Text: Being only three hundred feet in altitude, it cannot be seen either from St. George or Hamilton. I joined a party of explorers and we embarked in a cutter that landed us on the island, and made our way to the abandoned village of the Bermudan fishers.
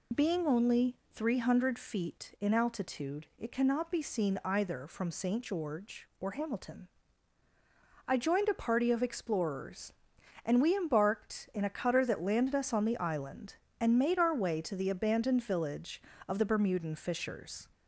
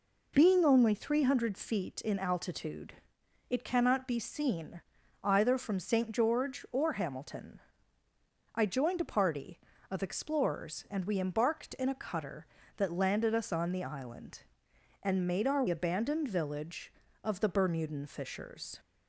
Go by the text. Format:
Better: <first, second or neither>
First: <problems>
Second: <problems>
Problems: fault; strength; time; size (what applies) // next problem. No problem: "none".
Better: first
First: none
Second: pauses between "seen" and "either"; at 4.8 s; 0.42 s long // skips "way to the"; at 15.6 s